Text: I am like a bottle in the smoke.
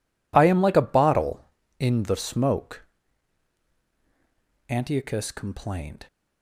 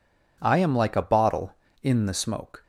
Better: second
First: goes on to say "Antiochus complained"; from 4.6 s on; 1.4 s long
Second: none

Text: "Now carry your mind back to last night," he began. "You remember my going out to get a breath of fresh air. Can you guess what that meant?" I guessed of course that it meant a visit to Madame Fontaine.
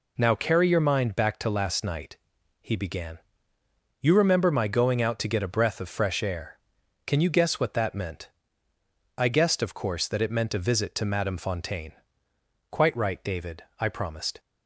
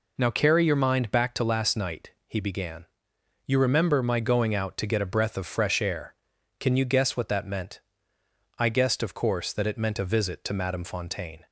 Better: second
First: goes on to say "Quite right David I promised"; strong; from 12.6 s on; 1.7 s long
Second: none

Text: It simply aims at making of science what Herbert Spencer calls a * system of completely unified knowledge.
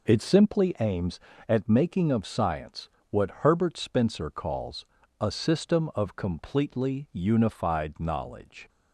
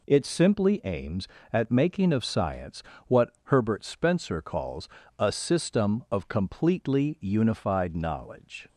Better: neither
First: pauses between "science" and "what"; slight; at 2.8 s; 0.22 s long // pauses between "calls" and "a"; slight; at 4.8 s; 0.34 s long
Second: pauses between "science" and "what"; slight; at 2.8 s; 0.26 s long // pauses between "calls" and "a"; slight; at 4.8 s; 0.30 s long

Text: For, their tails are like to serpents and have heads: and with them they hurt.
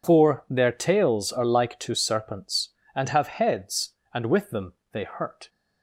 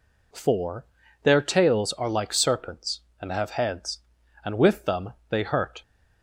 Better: first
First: pauses between "them" and "they"; slight; at 4.7 s; 0.18 s long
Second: skips "to"; at 2.3 s // pauses between "them" and "they"; slight; at 5.1 s; 0.16 s long

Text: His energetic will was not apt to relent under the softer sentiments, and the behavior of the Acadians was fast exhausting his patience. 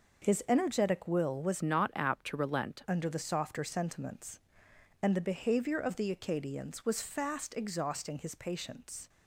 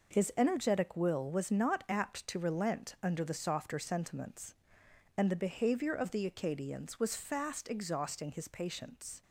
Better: second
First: changes voice from "not" to "relent"; from 1.6 to 2.8 s; 1.2 s long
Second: none

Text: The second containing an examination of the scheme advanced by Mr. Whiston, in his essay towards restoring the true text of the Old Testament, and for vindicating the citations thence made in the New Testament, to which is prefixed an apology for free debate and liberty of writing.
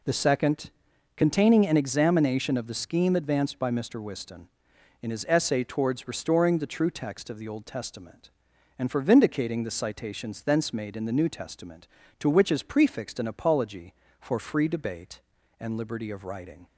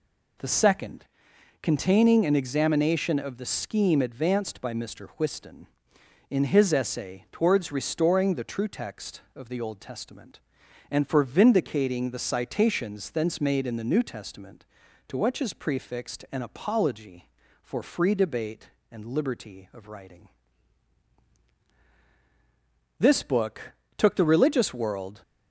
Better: first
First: pauses between "second" and "containing"; at 0.6 s; 0.44 s long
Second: pauses between "second" and "containing"; noticeable; at 1.0 s; 0.54 s long // goes on to say "This book took the religious world"; strong; from 22.9 s on; 2.2 s long

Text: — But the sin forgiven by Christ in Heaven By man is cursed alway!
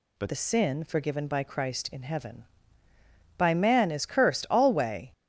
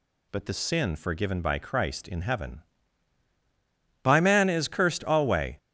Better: second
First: changes voice at "the"; from 0.2 s on; 4.9 s long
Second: none

